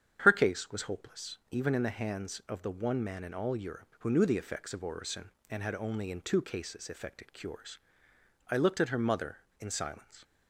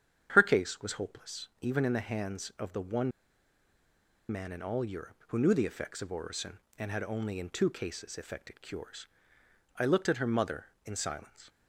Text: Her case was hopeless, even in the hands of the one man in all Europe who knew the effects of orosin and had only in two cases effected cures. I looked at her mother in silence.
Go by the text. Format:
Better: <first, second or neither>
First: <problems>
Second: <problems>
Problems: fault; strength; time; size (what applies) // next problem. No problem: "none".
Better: first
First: starts louder than the rest; strong; until 1.2 s; 8.5 dB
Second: starts louder than the rest; strong; until 1.3 s; 8.5 dB // pauses between "one" and "man"; at 3.1 s; 1.1 s long